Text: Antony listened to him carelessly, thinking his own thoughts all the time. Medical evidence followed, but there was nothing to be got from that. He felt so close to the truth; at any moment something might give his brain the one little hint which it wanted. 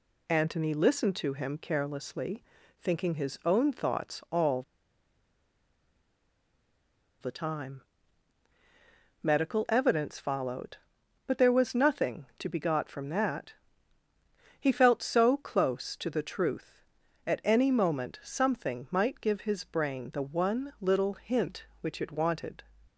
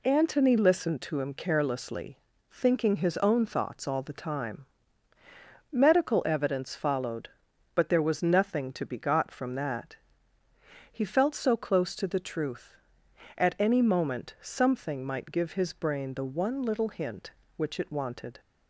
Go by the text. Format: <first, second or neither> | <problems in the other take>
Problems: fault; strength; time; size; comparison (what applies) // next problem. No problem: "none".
second | pauses between "all" and "the"; strong; at 4.6 s; 2.5 s long